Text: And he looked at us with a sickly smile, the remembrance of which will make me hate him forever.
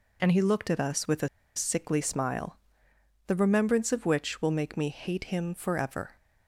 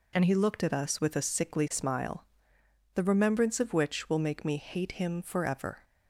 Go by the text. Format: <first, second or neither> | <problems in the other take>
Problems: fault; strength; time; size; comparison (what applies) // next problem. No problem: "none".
second | pauses between "a" and "sickly"; slight; at 1.2 s; 0.27 s long